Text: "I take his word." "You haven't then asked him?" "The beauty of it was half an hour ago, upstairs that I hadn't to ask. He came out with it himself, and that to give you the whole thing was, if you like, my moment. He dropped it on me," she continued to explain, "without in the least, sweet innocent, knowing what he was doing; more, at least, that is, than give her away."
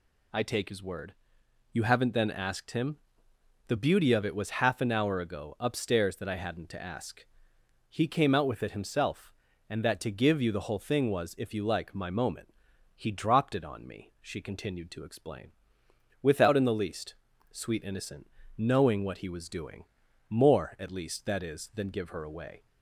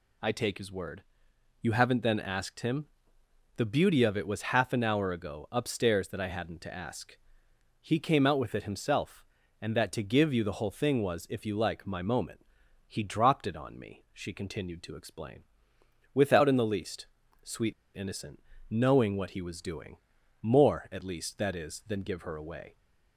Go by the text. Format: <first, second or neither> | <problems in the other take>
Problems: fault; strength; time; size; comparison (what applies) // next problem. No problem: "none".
first | pauses between "sweet" and "innocent"; slight; at 17.7 s; 0.21 s long